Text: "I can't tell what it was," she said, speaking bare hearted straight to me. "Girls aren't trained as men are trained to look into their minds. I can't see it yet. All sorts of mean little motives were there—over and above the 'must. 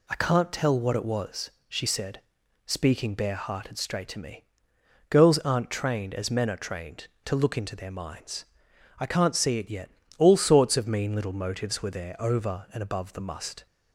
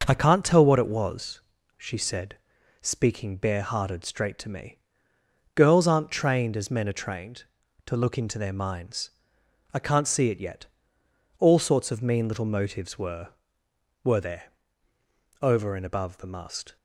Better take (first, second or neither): first